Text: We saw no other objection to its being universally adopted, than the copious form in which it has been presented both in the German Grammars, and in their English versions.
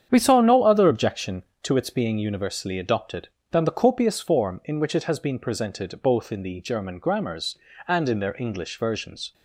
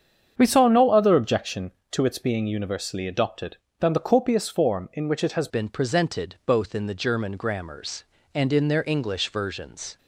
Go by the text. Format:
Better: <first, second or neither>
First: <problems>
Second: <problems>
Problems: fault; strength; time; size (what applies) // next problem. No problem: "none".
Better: first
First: starts louder than the rest; strong; until 1.1 s; 8.5 dB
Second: starts louder than the rest; strong; until 1.3 s; 7.5 dB // changes voice at "been"; from 5.4 s on; 4.5 s long